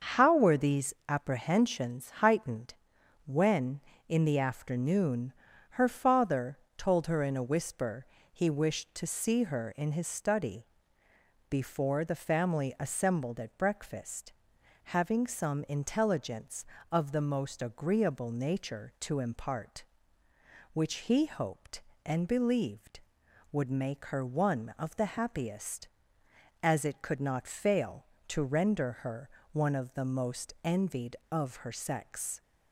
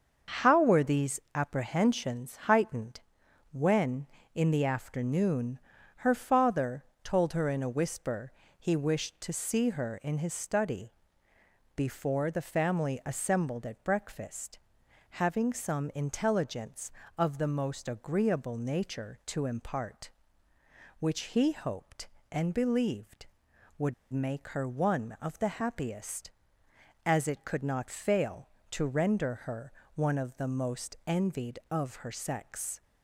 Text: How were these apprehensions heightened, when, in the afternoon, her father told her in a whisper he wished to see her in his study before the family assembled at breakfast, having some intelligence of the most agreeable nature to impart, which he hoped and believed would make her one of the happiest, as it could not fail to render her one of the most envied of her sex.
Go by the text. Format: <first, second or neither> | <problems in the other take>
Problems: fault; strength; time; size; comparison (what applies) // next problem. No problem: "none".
first | starts louder than the rest; until 1.4 s; 6.5 dB; also in the first // pauses between "these" and "apprehensions"; slight; at 1.1 s; 0.16 s long; slight in the first // pauses between "father" and "told"; slight; at 6.8 s; 0.18 s long; slight in the first // pauses between "whisper" and "he"; slight; at 8.3 s; 0.26 s long; slight in the first // pauses between "study" and "before"; noticeable; at 10.9 s; 0.82 s long; noticeable in the first // pauses between "would" and "make"; slight; at 23.9 s; 0.19 s long // pauses between "her" and "one"; slight; at 29.7 s; 0.22 s long; slight in the first